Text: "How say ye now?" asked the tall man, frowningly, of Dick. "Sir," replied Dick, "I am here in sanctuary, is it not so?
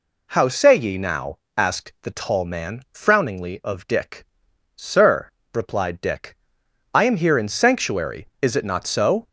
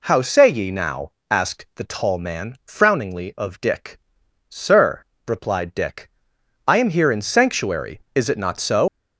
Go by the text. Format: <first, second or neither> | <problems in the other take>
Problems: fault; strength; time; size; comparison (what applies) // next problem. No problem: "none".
first | leaves "so" unfinished; at 8.8 s; 135 ms